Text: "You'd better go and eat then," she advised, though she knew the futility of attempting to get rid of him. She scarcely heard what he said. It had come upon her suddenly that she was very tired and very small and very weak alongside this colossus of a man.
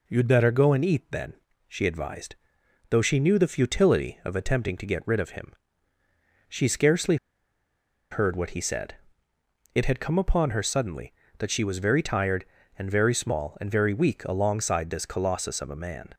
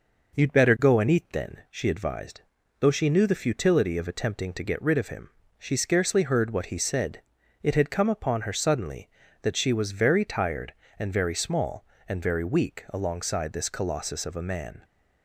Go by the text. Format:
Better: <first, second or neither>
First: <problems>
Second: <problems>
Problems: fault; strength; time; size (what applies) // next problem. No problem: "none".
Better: second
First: pauses between "scarcely" and "heard"; noticeable; at 7.1 s; 0.95 s long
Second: none